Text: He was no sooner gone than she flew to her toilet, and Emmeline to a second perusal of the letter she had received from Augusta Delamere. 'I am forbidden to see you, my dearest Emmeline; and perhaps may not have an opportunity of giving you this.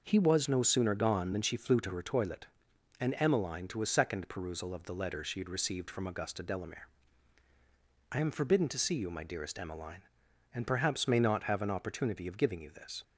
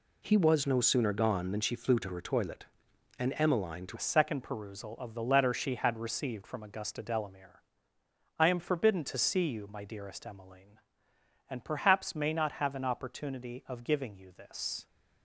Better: first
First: none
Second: changes voice at "a"; from 3.9 s on; 10.9 s long

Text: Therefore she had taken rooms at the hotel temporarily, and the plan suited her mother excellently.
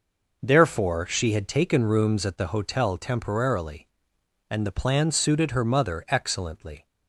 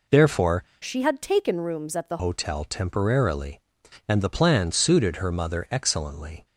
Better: first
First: none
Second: changes voice from "she" to "the"; from 0.8 to 2.1 s; 1.3 s long

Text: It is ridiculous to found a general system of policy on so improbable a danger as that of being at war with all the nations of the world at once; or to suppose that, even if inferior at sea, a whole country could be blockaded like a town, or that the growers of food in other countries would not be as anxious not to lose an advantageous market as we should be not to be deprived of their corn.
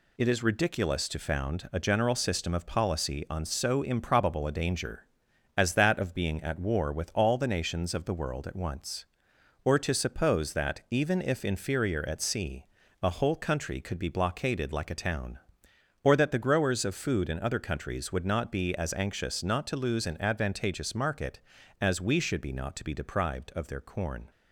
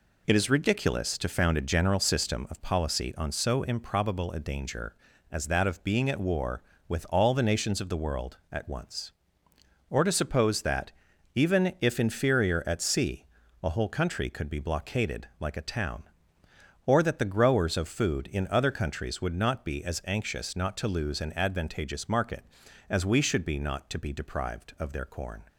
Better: neither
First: none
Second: none

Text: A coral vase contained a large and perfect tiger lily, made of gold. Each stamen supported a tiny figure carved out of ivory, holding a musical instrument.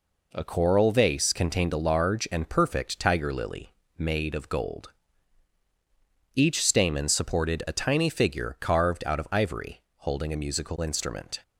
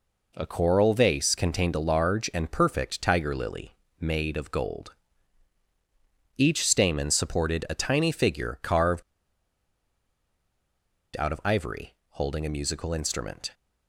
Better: first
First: none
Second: pauses between "carved" and "out"; strong; at 9.0 s; 2.1 s long

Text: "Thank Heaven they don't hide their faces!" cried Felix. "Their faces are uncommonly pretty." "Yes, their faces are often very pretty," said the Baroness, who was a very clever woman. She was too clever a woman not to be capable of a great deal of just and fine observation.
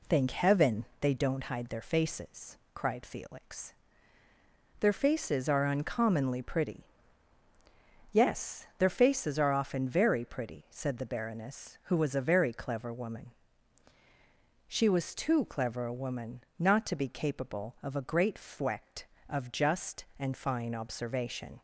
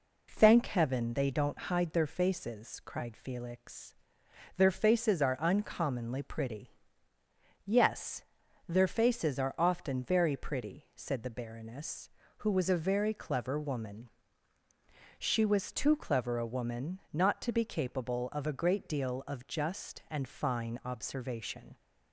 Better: second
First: pauses between "Heaven" and "they"; slight; at 0.8 s; 0.16 s long // pauses between "woman" and "not"; slight; at 16.4 s; 0.16 s long // says "fwect" for "deal"; at 18.3 s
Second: none

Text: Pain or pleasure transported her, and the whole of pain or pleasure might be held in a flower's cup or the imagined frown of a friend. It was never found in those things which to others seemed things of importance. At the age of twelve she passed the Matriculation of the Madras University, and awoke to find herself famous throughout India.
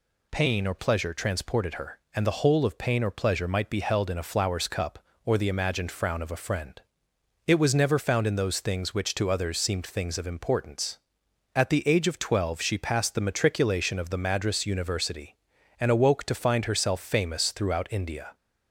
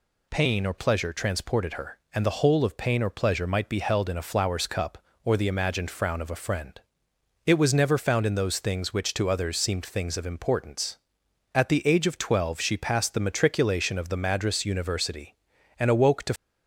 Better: first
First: none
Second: stops before "find herself famous throughout India"; at 16.3 s

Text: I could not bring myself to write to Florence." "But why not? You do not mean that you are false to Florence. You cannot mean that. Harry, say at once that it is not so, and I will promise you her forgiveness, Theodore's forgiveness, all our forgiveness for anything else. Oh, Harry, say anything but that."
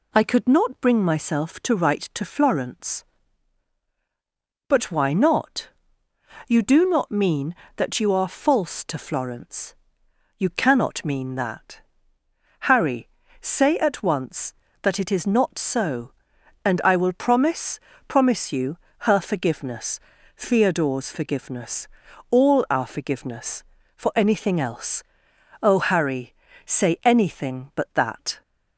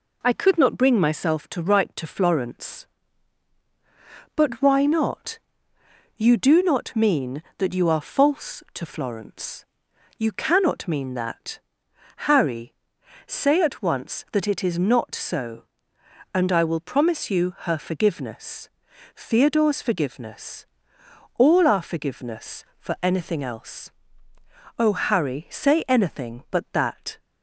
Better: second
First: says "promise" twice; at 18.0 s // pauses between "you" and "her"; slight; at 18.7 s; 0.30 s long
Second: none

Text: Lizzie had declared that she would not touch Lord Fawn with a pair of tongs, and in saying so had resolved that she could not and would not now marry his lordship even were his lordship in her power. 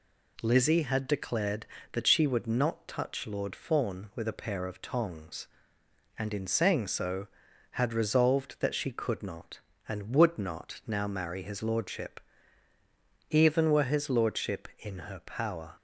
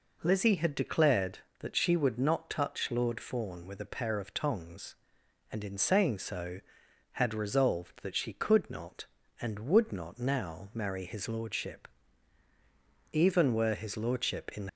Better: first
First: pauses between "lordship" and "even"; at 12.1 s; 1.1 s long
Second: pauses between "lordship" and "even"; strong; at 11.8 s; 1.2 s long // stops before "her power"; at 14.6 s

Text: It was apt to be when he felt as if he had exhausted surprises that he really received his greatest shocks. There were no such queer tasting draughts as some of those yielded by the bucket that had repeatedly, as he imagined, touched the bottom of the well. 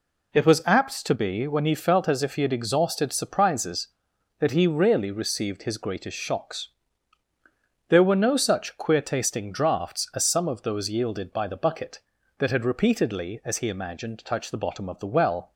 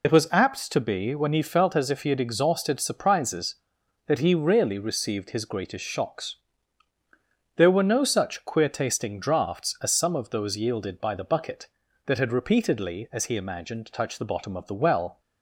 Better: first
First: none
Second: loses the start of "It"; at 0.0 s; 45 ms

